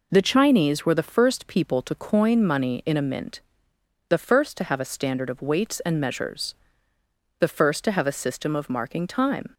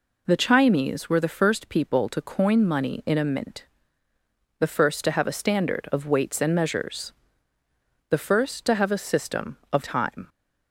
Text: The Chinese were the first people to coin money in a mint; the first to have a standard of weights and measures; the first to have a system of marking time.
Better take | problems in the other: first | skips "marking"; at 9.8 s

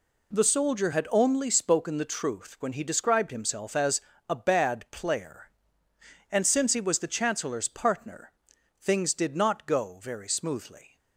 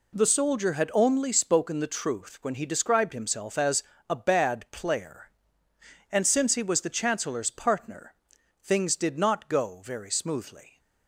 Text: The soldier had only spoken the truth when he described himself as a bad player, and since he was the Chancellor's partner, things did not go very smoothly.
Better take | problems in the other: neither | pauses between "as" and "a"; slight; the same in both

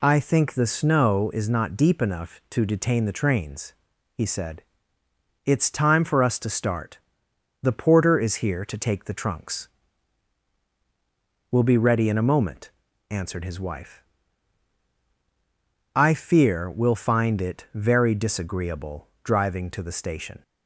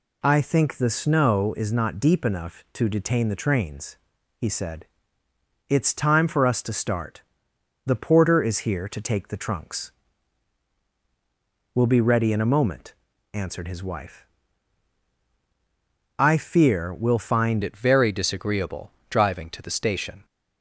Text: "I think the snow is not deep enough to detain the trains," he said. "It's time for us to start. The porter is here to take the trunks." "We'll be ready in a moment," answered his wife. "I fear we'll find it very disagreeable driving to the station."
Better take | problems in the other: first | changes voice at "it"; from 17.6 s on; 2.6 s long // pauses between "disagreeable" and "driving"; slight; at 18.9 s; 0.16 s long

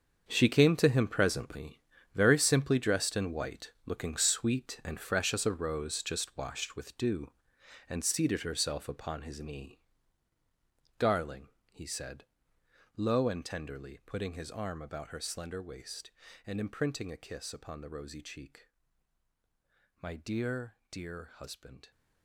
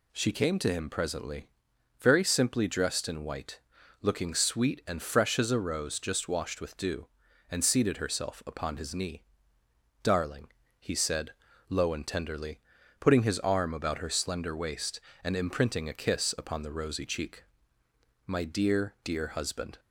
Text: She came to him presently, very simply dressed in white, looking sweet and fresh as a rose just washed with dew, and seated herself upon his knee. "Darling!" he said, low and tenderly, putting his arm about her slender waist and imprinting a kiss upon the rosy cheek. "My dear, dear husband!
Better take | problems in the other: second | gets quieter; strong; throughout; 13 dB

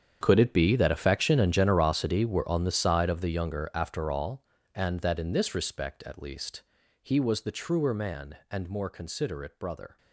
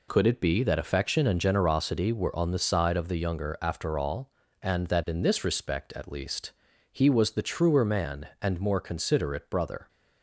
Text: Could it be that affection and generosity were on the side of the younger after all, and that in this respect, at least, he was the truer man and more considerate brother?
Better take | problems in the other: second | gets quieter; strong; throughout; 16.5 dB

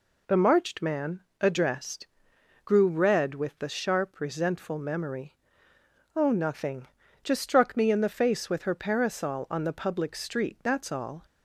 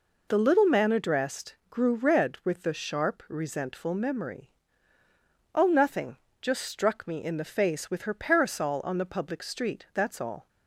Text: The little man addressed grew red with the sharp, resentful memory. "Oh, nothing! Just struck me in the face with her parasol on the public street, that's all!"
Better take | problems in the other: second | says "marched" for "little"; at 0.3 s // pauses between "man" and "addressed"; slight; at 1.2 s; 0.18 s long // pauses between "addressed" and "grew"; noticeable; at 2.0 s; 0.58 s long

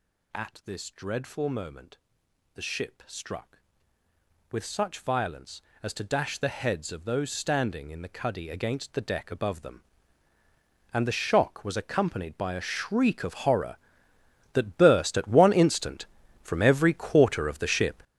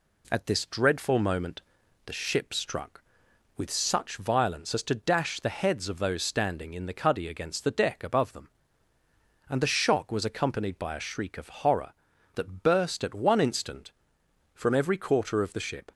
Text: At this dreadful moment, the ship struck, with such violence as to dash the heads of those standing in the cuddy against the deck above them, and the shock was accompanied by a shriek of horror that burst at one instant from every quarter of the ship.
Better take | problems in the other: second | gets louder; strong; throughout; 11.5 dB

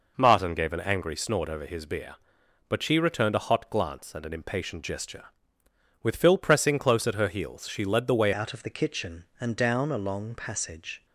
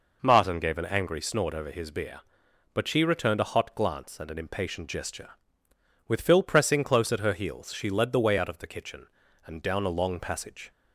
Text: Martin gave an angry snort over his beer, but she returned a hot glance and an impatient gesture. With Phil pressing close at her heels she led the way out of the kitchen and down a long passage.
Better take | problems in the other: second | changes voice at "out"; from 8.3 s on; 2.7 s long

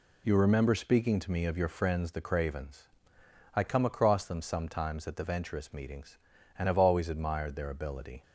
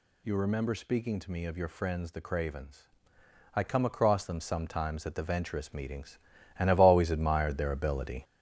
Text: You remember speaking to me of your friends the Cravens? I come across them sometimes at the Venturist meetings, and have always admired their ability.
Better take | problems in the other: first | gets louder; noticeable; throughout; 5.5 dB

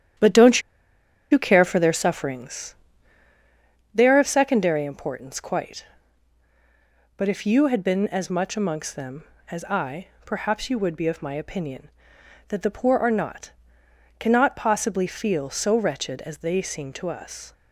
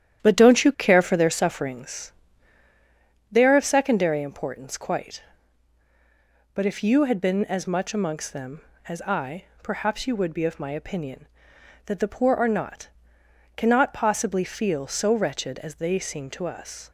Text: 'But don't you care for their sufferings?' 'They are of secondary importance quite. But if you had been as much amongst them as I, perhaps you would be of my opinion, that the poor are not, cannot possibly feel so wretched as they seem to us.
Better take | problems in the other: second | starts louder than the rest; strong; until 1.9 s; 10.5 dB; strong in the second // pauses between "don't" and "you"; noticeable; at 0.6 s; 0.70 s long

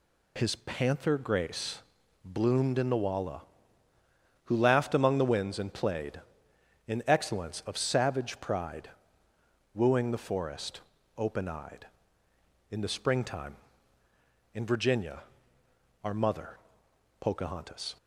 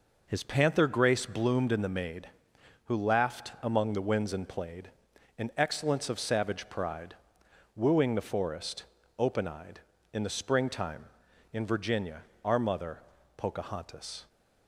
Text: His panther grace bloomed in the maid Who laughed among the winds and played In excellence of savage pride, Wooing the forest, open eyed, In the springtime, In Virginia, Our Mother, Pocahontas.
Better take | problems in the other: second | pauses between "grace" and "bloomed"; at 1.7 s; 0.44 s long // says "walla" for "maid"; at 3.0 s

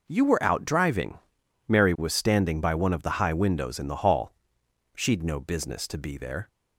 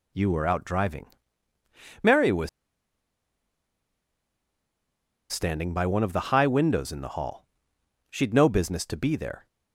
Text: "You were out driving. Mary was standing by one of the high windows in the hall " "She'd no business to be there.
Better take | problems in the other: first | pauses between "was" and "standing"; strong; at 2.4 s; 2.8 s long

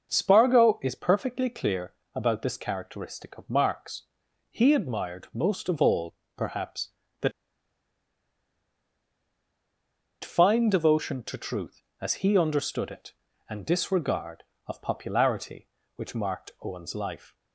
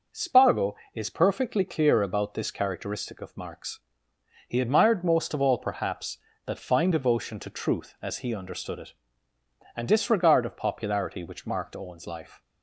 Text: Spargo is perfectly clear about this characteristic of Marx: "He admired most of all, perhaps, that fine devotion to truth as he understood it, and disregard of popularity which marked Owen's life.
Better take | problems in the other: second | starts louder than the rest; until 1.1 s; 6 dB // pauses between "clear" and "about"; slight; at 1.9 s; 0.24 s long // pauses between "that" and "fine"; strong; at 7.3 s; 2.9 s long

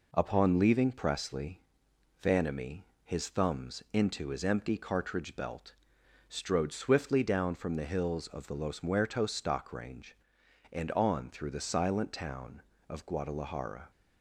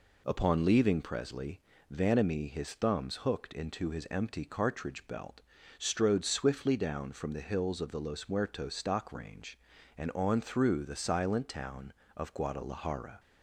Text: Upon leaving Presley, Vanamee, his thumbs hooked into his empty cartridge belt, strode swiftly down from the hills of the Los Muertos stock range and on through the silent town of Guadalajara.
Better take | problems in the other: second | skips "hooked"; at 3.8 s

